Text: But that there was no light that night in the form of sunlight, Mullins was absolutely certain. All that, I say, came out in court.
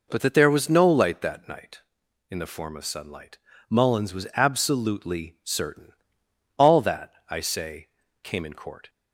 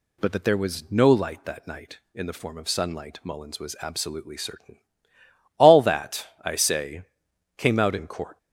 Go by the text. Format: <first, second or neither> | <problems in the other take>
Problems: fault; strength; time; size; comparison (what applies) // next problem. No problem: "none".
second | skips "out"; at 8.4 s